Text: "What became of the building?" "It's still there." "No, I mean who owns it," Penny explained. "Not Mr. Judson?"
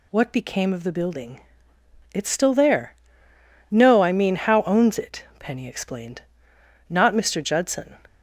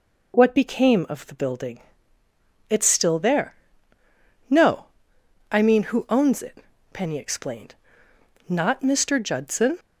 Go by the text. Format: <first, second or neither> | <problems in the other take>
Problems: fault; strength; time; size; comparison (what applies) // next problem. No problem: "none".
second | says "how" for "who"; at 4.3 s